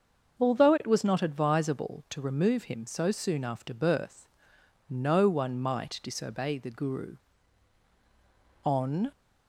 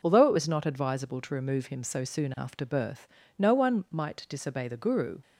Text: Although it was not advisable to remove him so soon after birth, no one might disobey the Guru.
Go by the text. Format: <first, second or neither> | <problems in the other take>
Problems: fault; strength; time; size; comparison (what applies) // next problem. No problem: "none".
second | starts louder than the rest; until 1.4 s; 6.5 dB // goes on to say "On"; slight; from 8.6 s on; 0.48 s long